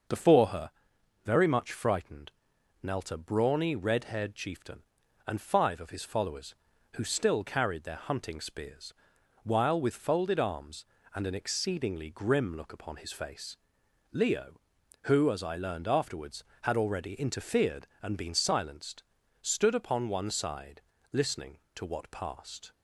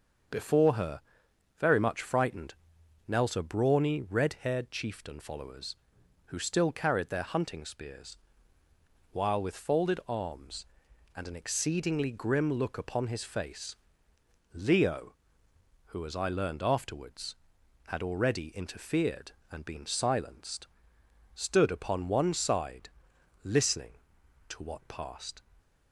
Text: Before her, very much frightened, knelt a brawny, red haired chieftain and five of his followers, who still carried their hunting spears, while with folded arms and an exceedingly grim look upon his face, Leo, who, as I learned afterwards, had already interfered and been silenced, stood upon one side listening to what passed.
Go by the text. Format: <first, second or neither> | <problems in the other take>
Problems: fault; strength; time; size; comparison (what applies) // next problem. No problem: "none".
first | starts louder than the rest; until 1.8 s; 6.5 dB; noticeable in the first // skips "and five of his"; at 5.1 s // pauses between "side" and "listening"; noticeable; at 22.8 s; 0.52 s long; slight in the first